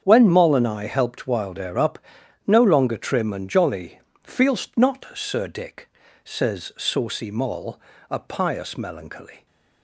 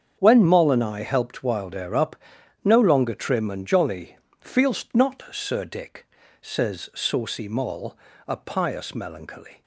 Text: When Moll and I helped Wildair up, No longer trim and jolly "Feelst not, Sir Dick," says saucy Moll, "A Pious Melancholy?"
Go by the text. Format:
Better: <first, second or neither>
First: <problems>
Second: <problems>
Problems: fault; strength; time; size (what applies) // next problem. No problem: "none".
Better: neither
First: starts louder than the rest; strong; until 1.0 s; 7.5 dB // pauses between "jolly" and "Feelst"; slight; at 3.9 s; 0.26 s long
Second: starts louder than the rest; strong; until 1.2 s; 7.5 dB // pauses between "jolly" and "Feelst"; slight; at 4.1 s; 0.26 s long